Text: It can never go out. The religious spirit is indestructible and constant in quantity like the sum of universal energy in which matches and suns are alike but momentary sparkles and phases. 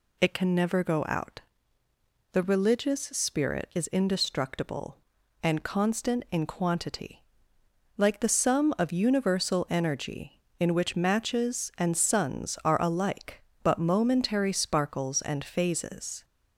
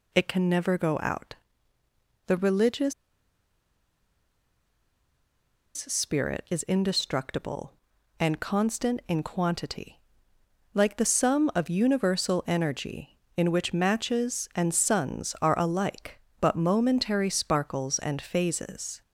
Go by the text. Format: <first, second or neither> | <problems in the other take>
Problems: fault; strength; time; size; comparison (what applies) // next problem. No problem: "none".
first | pauses between "religious" and "spirit"; strong; at 2.9 s; 2.8 s long // pauses between "quantity" and "like"; noticeable; at 9.9 s; 0.76 s long; noticeable in the first